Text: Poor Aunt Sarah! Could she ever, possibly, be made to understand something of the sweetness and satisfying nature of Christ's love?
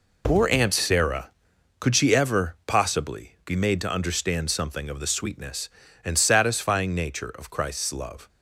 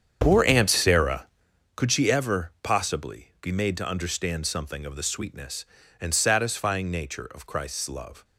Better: first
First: none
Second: starts louder than the rest; strong; until 1.5 s; 8 dB

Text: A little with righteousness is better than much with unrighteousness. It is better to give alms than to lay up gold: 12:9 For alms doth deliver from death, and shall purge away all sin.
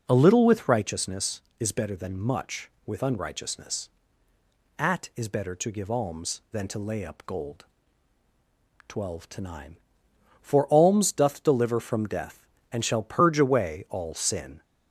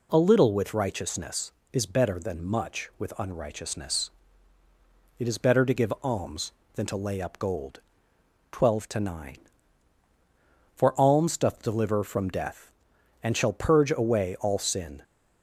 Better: second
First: says "At" for "It"; at 4.7 s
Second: none

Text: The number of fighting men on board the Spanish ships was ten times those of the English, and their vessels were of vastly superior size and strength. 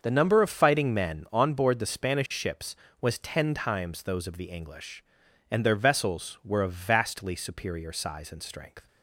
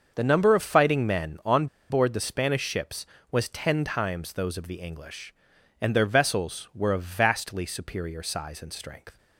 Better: first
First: starts louder than the rest; until 1.0 s; 6.5 dB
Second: starts louder than the rest; until 1.1 s; 6.5 dB // pauses between "on" and "board"; slight; at 1.6 s; 0.24 s long

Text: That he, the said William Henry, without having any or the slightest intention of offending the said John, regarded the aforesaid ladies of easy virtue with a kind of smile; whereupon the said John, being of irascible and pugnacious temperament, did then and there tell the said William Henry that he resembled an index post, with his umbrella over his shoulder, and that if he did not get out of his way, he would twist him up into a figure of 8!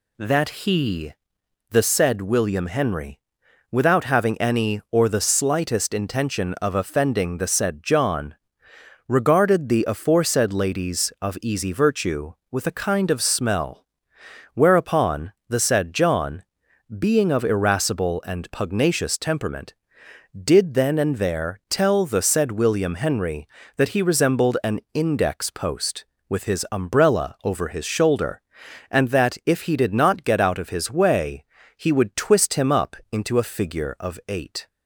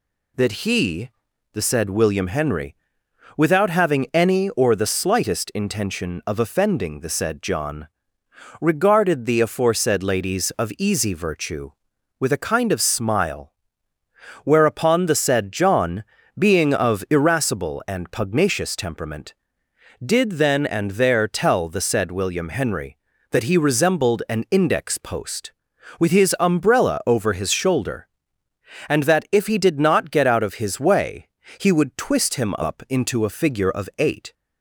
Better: second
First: says "smell" for "smile"; at 13.2 s // pauses between "whereupon" and "the"; slight; at 15.3 s; 0.16 s long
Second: none

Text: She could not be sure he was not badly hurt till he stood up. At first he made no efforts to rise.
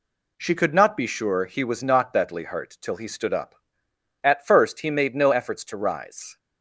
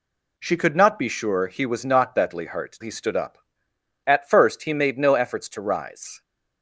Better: first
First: none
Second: skips "till"; at 2.7 s

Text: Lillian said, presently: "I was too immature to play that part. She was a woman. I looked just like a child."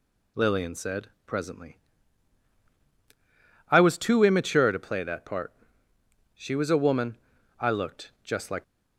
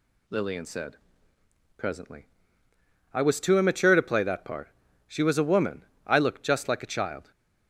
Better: second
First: stops before "a child"; at 8.6 s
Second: none

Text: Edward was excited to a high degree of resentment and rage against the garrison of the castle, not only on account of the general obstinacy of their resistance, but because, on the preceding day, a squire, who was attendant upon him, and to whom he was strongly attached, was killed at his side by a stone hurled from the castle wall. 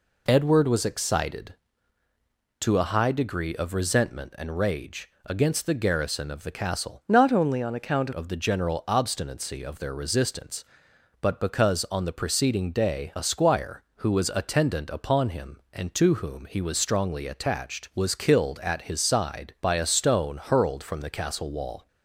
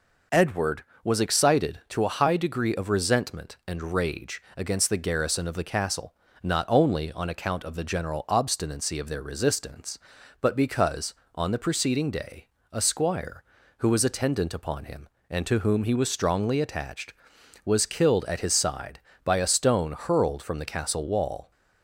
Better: second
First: pauses between "rage" and "against"; slight; at 5.0 s; 0.16 s long // changes voice from "not" to "account"; from 7.0 to 8.1 s; 1.1 s long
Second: pauses between "rage" and "against"; slight; at 4.4 s; 0.16 s long

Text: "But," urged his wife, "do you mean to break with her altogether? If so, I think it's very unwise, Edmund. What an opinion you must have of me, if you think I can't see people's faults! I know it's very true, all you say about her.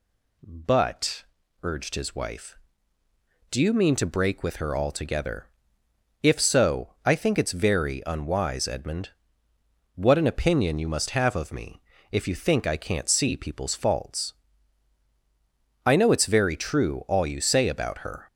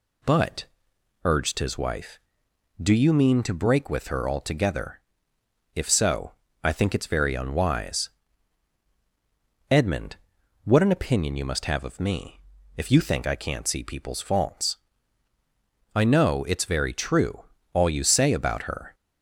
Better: neither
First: none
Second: none

